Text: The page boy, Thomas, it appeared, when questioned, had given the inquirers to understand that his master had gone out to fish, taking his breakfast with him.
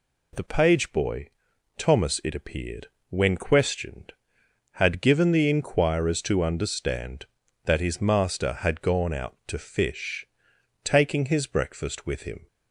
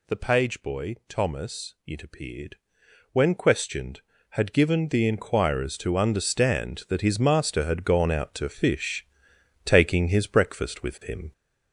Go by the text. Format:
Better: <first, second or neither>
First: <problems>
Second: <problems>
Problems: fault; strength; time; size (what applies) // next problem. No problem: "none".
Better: first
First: none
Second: gets louder; noticeable; throughout; 4 dB